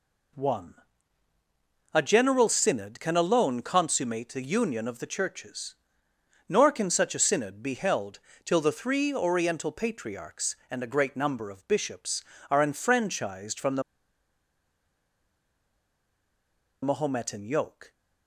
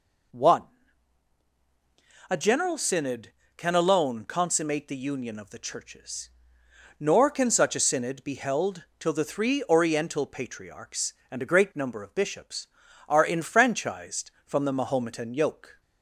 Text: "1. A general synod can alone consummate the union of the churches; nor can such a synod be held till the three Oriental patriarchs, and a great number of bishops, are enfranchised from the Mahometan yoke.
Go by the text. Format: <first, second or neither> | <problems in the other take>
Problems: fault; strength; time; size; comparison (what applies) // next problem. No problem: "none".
second | pauses between "held" and "till"; slight; at 8.1 s; 0.24 s long; slight in the second // pauses between "the" and "Mahometan"; strong; at 13.8 s; 3.0 s long